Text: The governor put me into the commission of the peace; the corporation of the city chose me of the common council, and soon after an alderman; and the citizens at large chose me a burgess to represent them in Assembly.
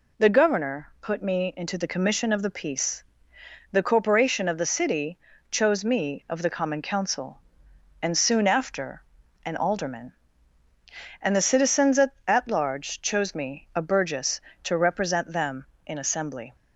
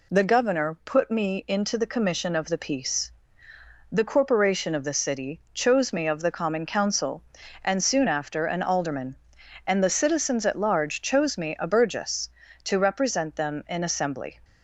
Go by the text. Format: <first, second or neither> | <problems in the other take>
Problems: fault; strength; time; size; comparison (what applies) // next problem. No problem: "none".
second | pauses between "city" and "chose"; slight; at 5.1 s; 0.32 s long // pauses between "after" and "an"; at 9.0 s; 0.42 s long // says "at" twice; at 12.2 s